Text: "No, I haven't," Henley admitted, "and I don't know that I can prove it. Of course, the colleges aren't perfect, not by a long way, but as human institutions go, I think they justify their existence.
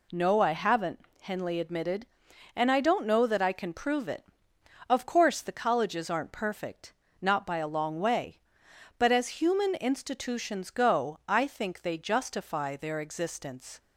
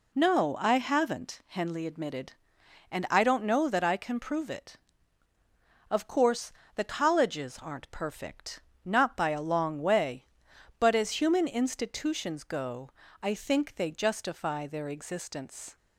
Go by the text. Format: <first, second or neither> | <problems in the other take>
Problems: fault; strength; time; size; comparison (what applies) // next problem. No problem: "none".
neither | none